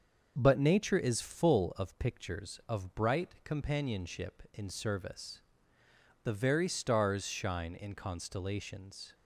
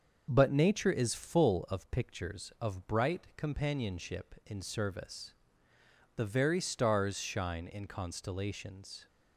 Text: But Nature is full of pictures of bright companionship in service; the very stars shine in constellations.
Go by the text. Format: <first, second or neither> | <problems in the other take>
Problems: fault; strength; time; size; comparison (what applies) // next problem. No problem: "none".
neither | starts louder than the rest; the same in both